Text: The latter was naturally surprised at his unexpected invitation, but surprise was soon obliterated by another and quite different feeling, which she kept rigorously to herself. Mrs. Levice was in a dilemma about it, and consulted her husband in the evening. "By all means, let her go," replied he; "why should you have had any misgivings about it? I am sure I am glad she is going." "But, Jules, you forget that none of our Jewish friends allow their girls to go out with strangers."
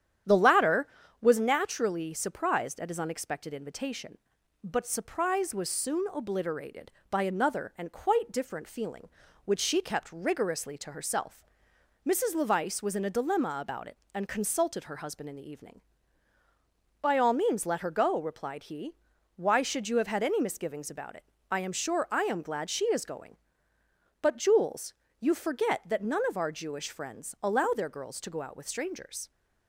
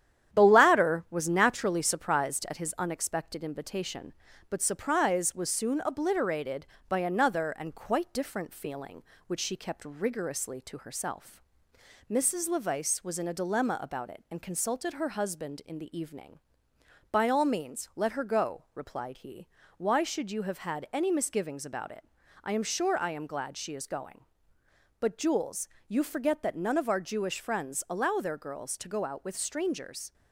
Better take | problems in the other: first | gets quieter; slight; throughout; 3.5 dB // starts louder than the rest; strong; until 1.4 s; 10 dB; strong in the first

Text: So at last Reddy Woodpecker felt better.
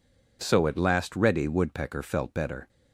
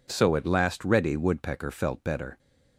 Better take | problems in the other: neither | none

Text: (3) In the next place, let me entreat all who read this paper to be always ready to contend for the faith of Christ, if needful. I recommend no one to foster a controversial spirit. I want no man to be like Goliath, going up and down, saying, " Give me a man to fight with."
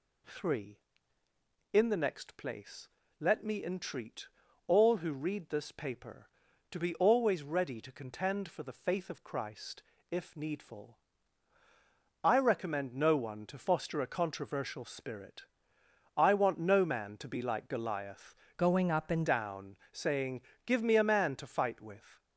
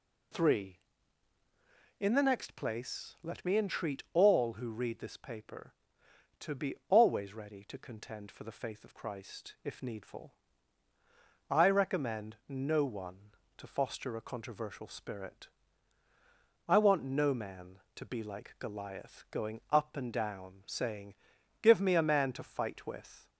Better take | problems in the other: second | pauses between "entreat" and "all"; at 4.2 s; 0.40 s long // changes voice from "going" to "and"; from 18.5 to 19.2 s; 0.7 s long

